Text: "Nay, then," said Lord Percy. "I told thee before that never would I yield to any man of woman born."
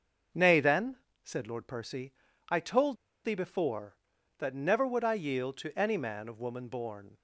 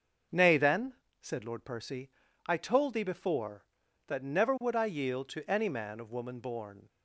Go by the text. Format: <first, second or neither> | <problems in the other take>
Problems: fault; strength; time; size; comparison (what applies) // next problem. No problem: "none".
second | starts louder than the rest; until 1.6 s; 6 dB; also in the second // pauses between "told" and "thee"; slight; at 2.9 s; 0.28 s long